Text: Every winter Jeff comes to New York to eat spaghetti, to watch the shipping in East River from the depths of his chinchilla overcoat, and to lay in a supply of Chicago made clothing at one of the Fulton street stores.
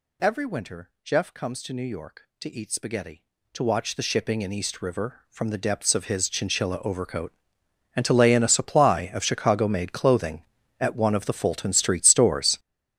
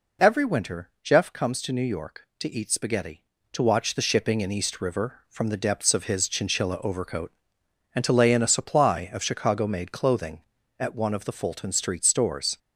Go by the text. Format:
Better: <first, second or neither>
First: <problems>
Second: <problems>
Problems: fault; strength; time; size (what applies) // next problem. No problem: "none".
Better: second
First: gets louder; strong; throughout; 13 dB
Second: none